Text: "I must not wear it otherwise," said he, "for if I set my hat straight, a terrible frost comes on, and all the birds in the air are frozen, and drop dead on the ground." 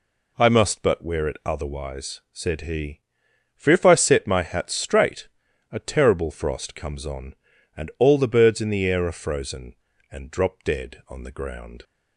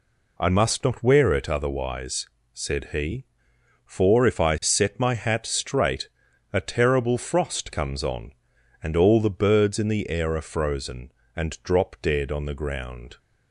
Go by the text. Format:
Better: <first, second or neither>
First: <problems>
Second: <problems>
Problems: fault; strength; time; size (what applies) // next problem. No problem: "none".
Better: second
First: says "but" for "not"; at 0.8 s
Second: none